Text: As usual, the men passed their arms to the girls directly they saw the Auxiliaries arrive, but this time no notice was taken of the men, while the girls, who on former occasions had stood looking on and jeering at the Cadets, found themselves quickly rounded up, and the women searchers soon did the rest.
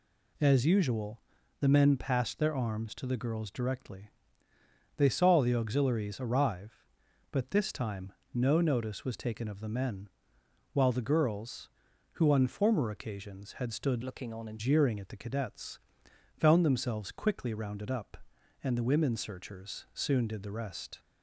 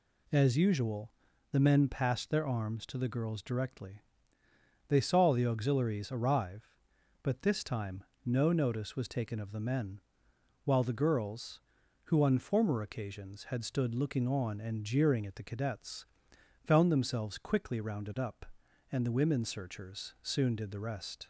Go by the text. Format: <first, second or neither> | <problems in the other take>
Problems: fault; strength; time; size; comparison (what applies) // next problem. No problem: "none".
second | pauses between "directly" and "they"; noticeable; at 4.1 s; 0.86 s long; noticeable in the second // pauses between "time" and "no"; slight; at 8.1 s; 0.20 s long; slight in the second // changes voice from "looking" to "and"; from 14.0 to 14.6 s; 0.6 s long